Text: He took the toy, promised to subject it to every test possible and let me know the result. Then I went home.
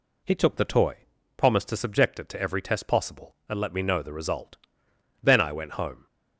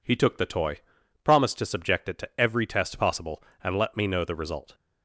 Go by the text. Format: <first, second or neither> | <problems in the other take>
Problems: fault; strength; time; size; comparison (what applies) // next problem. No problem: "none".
first | stops before "Then I went home"; at 4.7 s